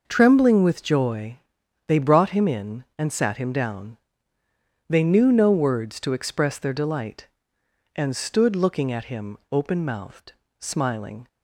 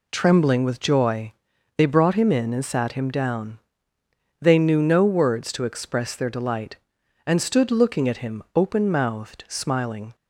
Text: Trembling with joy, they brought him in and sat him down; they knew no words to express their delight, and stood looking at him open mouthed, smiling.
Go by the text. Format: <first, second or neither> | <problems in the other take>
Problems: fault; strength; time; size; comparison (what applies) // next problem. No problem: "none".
neither | none